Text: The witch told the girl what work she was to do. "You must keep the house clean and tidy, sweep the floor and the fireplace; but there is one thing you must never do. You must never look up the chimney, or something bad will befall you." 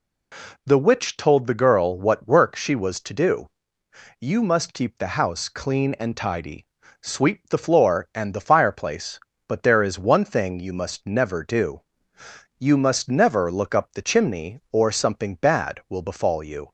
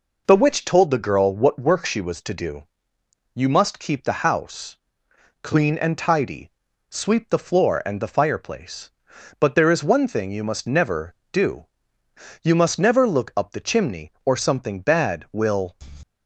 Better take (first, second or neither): first